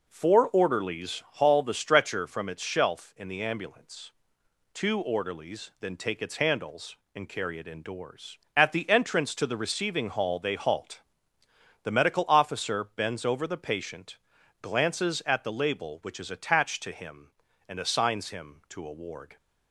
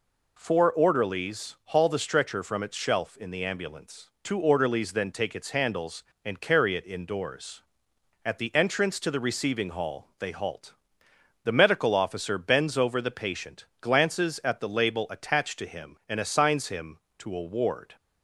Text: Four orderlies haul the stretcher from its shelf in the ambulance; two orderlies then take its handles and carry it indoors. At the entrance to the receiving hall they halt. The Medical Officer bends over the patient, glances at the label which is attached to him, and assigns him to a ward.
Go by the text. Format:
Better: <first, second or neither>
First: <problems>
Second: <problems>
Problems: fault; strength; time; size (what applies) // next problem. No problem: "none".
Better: first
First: none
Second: skips "which is"; at 15.0 s